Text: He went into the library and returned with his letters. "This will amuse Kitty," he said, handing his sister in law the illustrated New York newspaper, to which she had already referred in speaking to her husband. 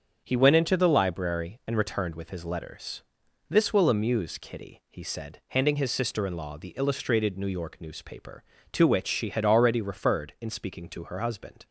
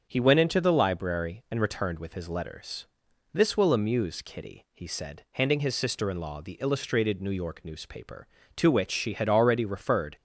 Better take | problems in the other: first | starts louder than the rest; strong; until 1.1 s; 7 dB; strong in the first // stops before "in speaking to her husband"; at 10.1 s

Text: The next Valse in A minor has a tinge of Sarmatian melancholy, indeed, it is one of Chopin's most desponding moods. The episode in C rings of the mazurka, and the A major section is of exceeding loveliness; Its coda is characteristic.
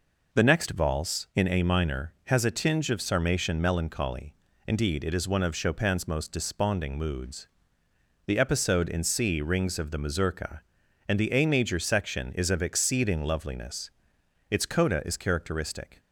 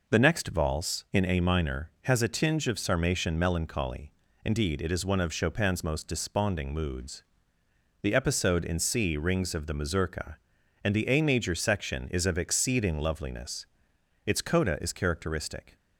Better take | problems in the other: neither | none

